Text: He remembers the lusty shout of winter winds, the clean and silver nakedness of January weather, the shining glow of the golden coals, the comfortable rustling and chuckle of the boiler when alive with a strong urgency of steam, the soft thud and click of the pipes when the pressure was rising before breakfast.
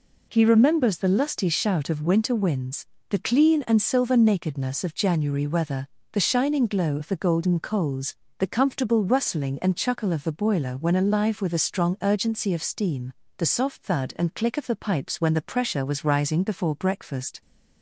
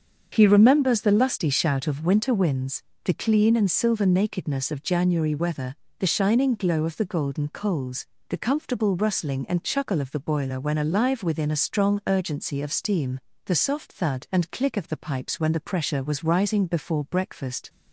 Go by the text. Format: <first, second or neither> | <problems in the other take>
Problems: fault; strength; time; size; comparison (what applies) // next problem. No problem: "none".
first | starts louder than the rest; until 1.3 s; 7 dB // says "within" for "with"; at 11.2 s